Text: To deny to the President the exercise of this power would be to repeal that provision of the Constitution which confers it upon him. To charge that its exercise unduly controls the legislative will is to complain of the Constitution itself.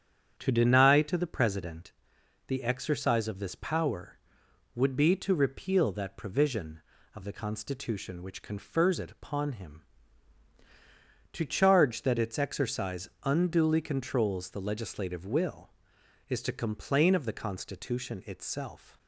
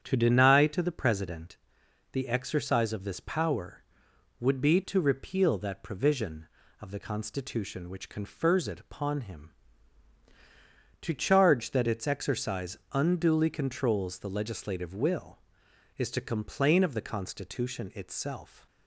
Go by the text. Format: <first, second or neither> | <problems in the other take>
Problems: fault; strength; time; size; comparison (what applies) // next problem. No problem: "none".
neither | starts louder than the rest; strong; the same in both // pauses between "President" and "the"; noticeable; the same in both